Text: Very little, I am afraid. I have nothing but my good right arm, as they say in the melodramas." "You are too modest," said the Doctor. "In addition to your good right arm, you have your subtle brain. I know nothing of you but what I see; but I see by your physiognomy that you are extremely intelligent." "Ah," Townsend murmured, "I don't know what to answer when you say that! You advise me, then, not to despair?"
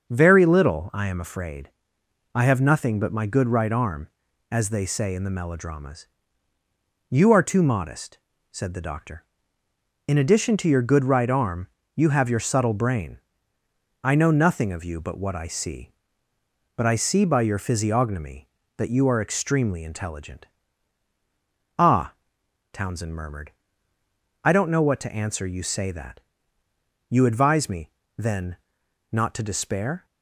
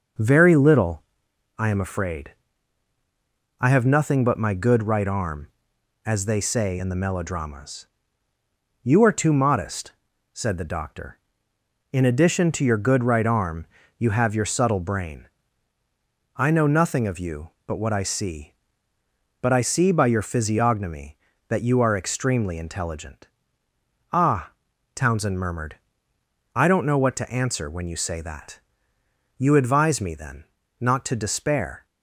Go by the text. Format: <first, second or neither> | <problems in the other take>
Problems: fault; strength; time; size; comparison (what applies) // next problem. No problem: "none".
second | starts louder than the rest; until 1.1 s; 6.5 dB; noticeable in the second // skips "when"; at 25.4 s